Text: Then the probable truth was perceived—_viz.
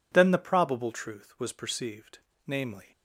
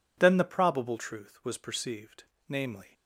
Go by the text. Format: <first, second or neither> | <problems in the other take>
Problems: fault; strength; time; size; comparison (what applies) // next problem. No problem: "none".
neither | none